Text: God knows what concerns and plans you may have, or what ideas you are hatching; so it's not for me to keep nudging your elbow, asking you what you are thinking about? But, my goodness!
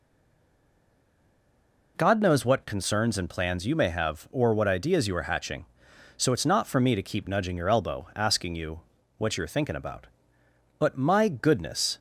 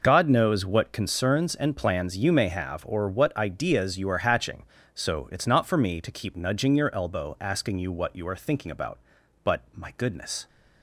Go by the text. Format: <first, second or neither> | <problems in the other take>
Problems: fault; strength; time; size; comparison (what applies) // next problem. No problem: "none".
second | stays silent before the first word; noticeable; until 1.9 s; 1.9 s long // pauses between "you" and "what"; slight; at 8.8 s; 0.36 s long